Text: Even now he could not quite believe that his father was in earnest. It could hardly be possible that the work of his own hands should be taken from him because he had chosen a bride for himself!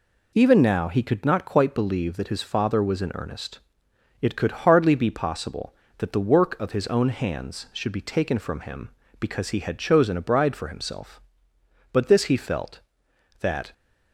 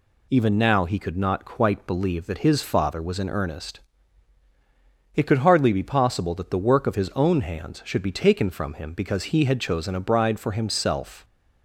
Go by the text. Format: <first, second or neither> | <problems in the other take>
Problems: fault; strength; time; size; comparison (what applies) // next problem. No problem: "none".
second | goes on to say "But this he felt that"; strong; from 11.9 s on; 1.8 s long